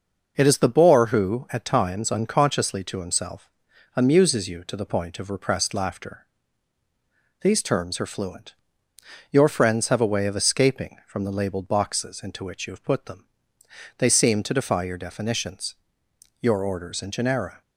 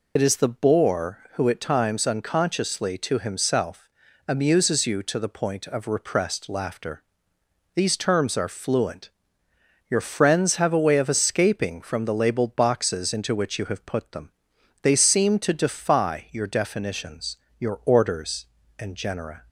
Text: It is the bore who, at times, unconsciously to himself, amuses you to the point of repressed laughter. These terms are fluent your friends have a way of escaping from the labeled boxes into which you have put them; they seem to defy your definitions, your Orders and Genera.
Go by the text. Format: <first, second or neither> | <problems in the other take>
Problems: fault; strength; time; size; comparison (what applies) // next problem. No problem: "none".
first | loses the start of "It"; at 0.1 s; 55 ms // pauses between "fluent" and "your"; noticeable; at 9.1 s; 0.78 s long; noticeable in the first